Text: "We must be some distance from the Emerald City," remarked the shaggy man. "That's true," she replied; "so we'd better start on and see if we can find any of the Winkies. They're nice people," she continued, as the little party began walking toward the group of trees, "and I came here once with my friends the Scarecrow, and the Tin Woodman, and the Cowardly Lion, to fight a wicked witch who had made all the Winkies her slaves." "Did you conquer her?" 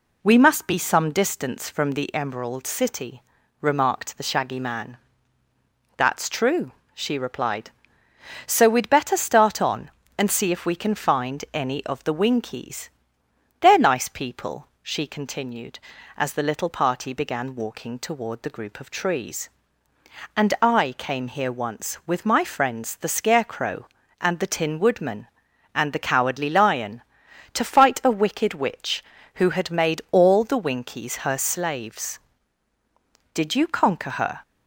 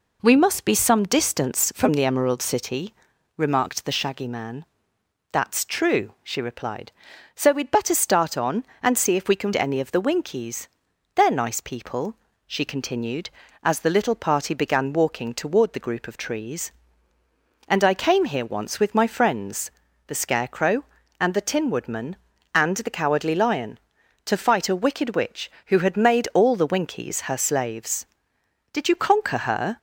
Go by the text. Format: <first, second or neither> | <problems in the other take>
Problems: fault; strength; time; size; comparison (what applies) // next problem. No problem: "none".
first | skips "find"; at 9.5 s // pauses between "friends" and "the"; slight; at 19.6 s; 0.36 s long